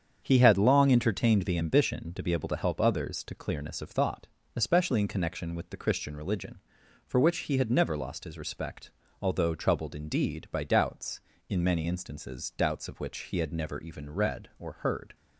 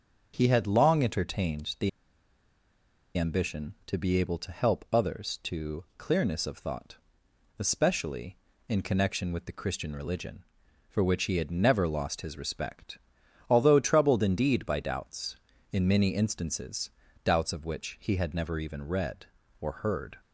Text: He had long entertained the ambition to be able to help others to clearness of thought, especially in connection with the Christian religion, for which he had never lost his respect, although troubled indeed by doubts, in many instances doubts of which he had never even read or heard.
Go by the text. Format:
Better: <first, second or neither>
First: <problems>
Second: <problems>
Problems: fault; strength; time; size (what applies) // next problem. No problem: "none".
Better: first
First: starts louder than the rest; strong; until 1.2 s; 7.5 dB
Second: starts louder than the rest; until 1.3 s; 6.5 dB // pauses between "the" and "ambition"; strong; at 1.8 s; 1.2 s long // pauses between "instances" and "doubts"; slight; at 16.8 s; 0.36 s long